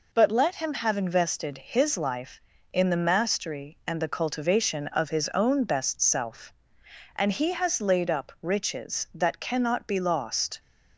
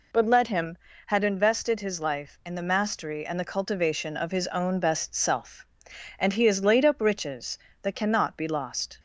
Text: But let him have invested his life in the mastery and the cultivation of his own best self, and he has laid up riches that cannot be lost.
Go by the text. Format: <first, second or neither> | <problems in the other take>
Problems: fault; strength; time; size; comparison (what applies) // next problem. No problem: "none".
first | says "had" for "have"; at 1.0 s